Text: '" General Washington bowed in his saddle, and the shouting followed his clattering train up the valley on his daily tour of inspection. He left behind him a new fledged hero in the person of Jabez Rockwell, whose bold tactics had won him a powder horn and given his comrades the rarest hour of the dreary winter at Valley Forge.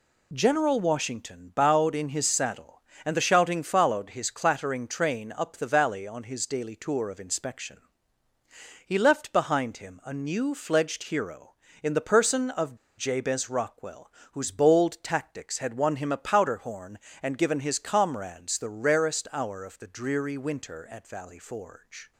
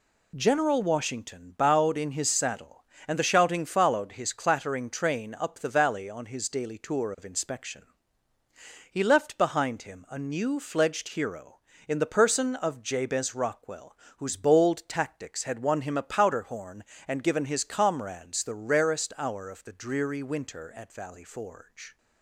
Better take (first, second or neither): second